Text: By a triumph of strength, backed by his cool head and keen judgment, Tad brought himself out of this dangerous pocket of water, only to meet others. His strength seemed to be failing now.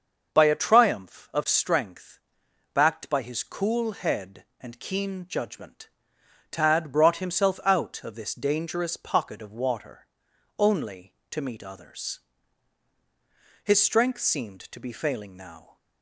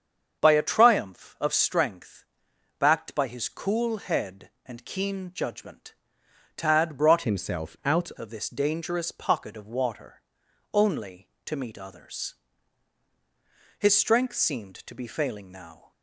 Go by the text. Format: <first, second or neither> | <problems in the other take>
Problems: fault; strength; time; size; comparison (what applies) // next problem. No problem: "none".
first | starts louder than the rest; until 1.4 s; 7 dB; also in the first // changes voice from "himself" to "out"; from 7.2 to 8.0 s; 0.8 s long